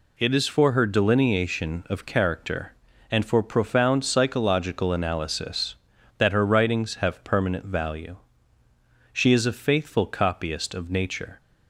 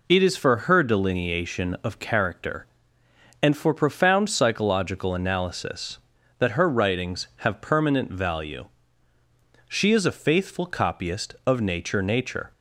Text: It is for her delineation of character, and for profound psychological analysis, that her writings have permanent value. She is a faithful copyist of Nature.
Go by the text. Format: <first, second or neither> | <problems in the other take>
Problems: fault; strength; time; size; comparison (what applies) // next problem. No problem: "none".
first | says "Nature" twice; at 12.0 s